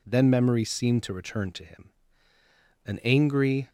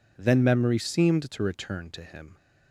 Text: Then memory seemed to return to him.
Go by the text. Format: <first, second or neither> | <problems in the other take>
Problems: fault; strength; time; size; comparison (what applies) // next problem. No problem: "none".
second | goes on to say "An angry"; noticeable; from 2.8 s on; 0.84 s long